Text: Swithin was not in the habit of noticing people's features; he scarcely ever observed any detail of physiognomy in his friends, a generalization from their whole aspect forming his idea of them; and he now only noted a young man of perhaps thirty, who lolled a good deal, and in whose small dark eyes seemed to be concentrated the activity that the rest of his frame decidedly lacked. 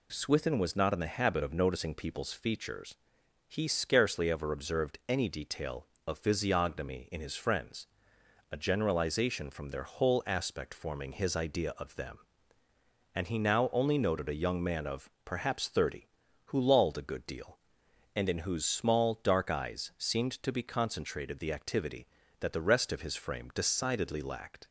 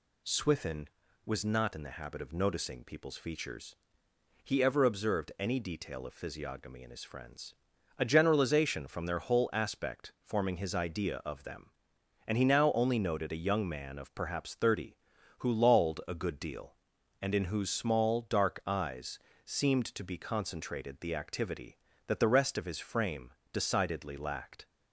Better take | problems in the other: first | skips "scarcely"; at 4.6 s // pauses between "eyes" and "seemed"; slight; at 19.1 s; 0.24 s long // pauses between "frame" and "decidedly"; slight; at 23.3 s; 0.18 s long

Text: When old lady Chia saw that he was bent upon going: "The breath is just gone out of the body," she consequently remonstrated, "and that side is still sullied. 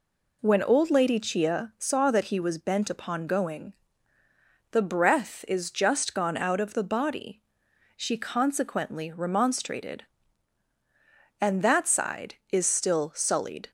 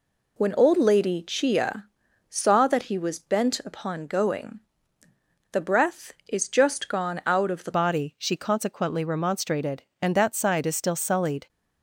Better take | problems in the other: first | pauses between "Chia" and "saw"; at 1.8 s; 0.42 s long // changes voice at "body"; from 7.7 s on; 3.7 s long

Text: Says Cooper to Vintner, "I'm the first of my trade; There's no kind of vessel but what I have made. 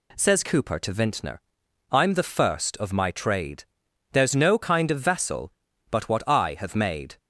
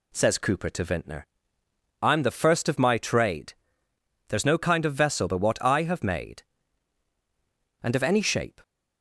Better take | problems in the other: first | goes on to say "And of any shape"; noticeable; from 7.8 s on; 0.80 s long

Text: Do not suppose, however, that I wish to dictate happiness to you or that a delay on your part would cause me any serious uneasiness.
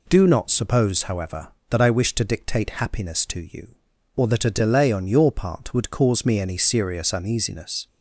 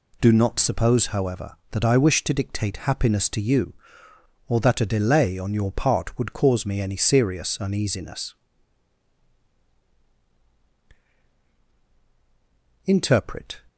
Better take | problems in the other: first | goes on to say "Interpret"; noticeable; from 12.8 s on; 0.80 s long

